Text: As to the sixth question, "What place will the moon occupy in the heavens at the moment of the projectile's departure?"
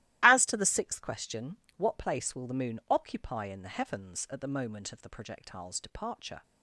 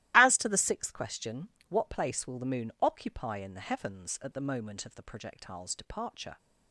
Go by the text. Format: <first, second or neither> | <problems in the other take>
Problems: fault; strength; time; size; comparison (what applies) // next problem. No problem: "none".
neither | starts louder than the rest; strong; the same in both